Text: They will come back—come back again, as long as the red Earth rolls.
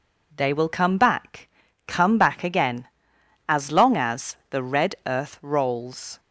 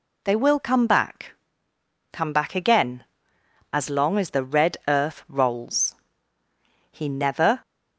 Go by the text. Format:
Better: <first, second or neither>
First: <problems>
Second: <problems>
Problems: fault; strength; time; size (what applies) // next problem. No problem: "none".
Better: first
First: none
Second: goes on to say "He never"; noticeable; from 6.9 s on; 0.70 s long